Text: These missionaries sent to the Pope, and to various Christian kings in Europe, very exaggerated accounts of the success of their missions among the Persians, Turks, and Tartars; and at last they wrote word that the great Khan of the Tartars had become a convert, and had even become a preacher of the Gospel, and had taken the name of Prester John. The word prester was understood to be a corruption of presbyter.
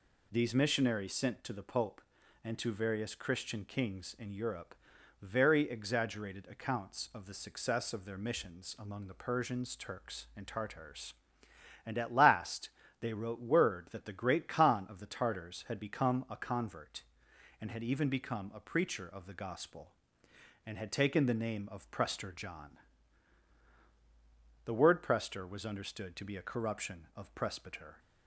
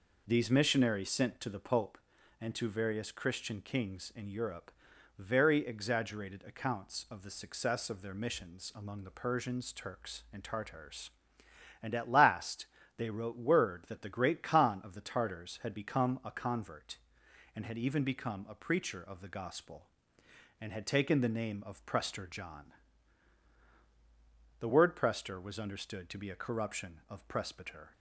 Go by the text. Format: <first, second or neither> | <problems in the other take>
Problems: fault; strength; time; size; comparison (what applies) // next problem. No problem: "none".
first | starts louder than the rest; noticeable; until 2.1 s; 4.5 dB // pauses between "last" and "they"; slight; at 12.6 s; 0.30 s long; slight in the first